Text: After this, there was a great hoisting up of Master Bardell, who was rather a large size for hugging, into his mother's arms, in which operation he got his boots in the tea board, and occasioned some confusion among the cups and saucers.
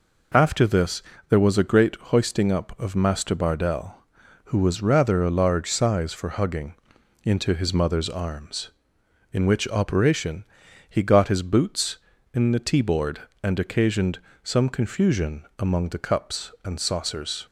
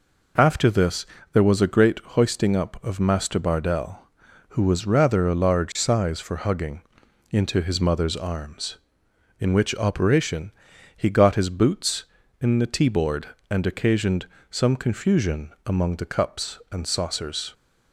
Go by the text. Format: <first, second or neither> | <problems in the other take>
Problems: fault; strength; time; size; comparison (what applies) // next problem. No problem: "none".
neither | pauses between "operation" and "he"; the same in both // pauses between "occasioned" and "some"; slight; the same in both